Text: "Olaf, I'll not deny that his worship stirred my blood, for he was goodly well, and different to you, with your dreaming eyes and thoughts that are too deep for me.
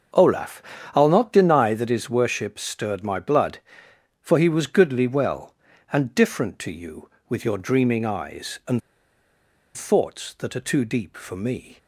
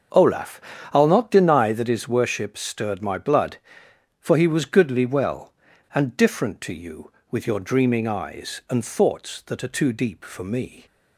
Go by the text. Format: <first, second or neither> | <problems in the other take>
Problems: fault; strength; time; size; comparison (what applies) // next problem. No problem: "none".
second | starts louder than the rest; until 1.4 s; 7 dB; also in the second // pauses between "and" and "thoughts"; noticeable; at 8.8 s; 0.97 s long